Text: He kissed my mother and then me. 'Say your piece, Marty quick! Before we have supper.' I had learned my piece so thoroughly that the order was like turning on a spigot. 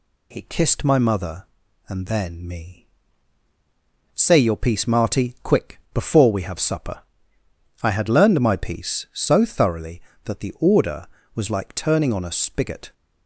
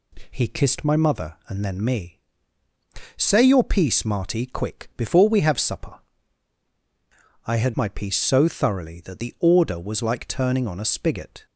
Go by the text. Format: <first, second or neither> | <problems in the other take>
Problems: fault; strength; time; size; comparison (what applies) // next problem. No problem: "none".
first | skips "learned"; at 7.7 s